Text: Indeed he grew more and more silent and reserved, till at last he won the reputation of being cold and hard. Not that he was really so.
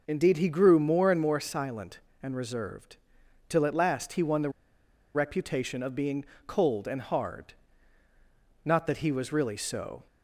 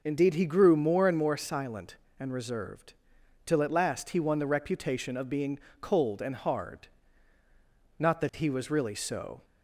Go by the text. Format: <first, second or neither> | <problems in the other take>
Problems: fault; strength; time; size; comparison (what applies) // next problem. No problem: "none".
second | pauses between "the" and "reputation"; noticeable; at 4.4 s; 0.65 s long // pauses between "being" and "cold"; slight; at 6.2 s; 0.22 s long; slight in the second